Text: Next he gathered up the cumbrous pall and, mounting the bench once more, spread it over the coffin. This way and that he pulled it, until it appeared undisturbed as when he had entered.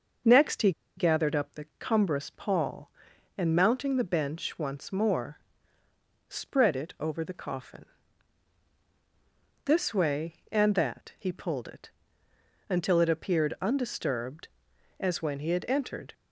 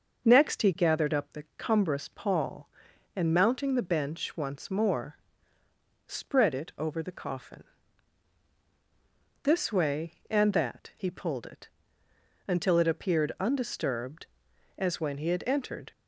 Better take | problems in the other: second | starts louder than the rest; until 1.5 s; 6 dB; also in the second // pauses between "he" and "gathered"; slight; at 0.7 s; 0.25 s long

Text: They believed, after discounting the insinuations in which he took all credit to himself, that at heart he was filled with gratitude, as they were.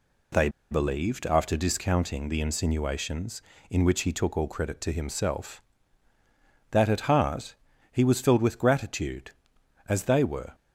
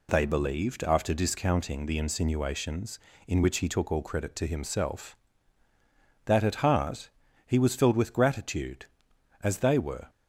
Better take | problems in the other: second | pauses between "They" and "believed"; slight; at 0.4 s; 0.21 s long // pauses between "heart" and "he"; slight; at 7.5 s; 0.36 s long; slight in the second

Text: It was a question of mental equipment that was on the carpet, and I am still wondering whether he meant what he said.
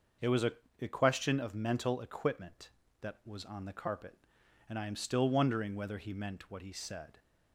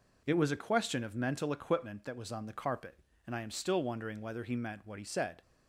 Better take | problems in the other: second | starts louder than the rest; until 1.4 s; 6 dB // says "a" twice; at 0.8 s

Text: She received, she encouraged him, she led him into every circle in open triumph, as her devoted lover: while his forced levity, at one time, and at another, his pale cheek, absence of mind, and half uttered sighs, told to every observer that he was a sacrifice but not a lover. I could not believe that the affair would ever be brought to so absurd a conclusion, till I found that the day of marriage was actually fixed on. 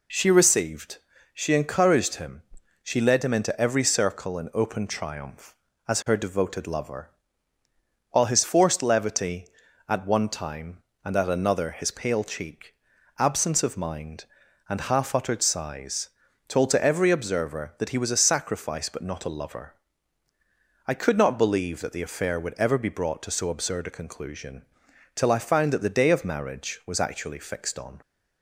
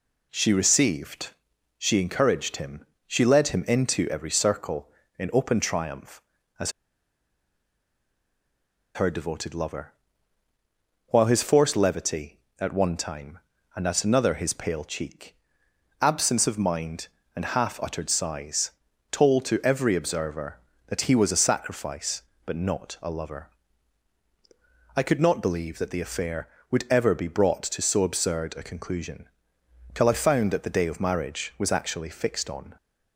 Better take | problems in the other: first | pauses between "as" and "her"; strong; at 6.7 s; 2.2 s long

